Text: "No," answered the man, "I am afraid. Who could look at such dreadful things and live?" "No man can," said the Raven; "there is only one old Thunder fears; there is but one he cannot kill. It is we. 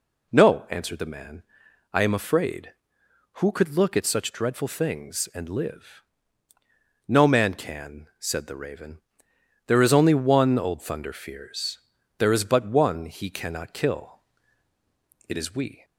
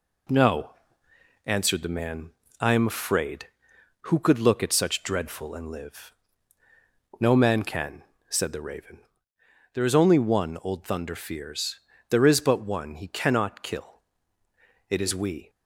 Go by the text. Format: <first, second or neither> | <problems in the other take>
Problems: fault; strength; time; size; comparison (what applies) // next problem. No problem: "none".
first | skips "things"; at 5.5 s